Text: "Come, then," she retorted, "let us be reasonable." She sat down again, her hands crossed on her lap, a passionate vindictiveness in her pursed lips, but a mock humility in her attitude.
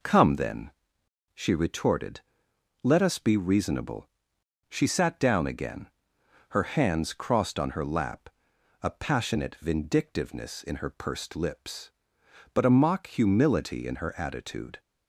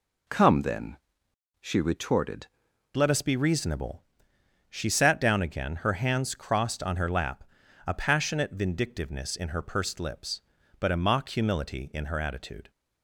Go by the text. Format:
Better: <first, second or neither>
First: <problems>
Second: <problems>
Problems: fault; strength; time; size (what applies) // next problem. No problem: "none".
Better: first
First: none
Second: changes voice at "let"; from 2.9 s on; 9.7 s long